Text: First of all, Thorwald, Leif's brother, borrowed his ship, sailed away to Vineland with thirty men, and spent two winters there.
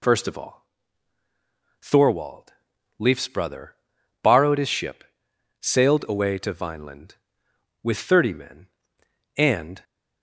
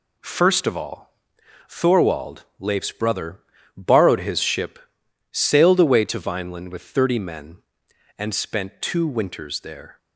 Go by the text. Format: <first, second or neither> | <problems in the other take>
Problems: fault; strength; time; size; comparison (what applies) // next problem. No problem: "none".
second | stops before "spent two winters there"; at 9.8 s